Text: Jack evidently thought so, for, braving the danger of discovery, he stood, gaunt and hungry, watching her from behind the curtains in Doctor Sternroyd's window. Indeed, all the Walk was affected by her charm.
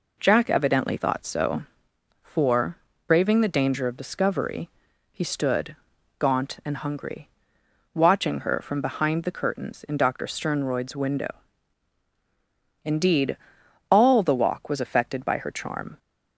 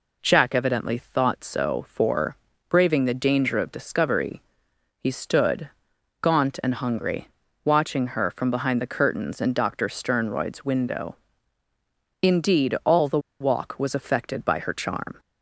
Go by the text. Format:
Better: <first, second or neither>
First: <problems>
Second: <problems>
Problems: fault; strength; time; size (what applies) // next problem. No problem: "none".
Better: first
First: none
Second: pauses between "the" and "Walk"; slight; at 13.1 s; 0.21 s long